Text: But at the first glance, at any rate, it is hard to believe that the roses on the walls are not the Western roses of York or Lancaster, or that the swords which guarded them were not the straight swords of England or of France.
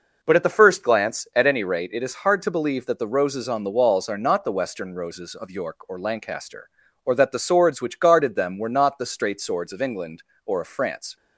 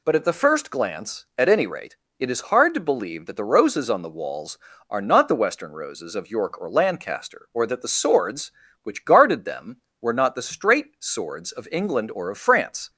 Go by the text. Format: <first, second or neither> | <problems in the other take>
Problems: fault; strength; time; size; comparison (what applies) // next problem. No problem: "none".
neither | none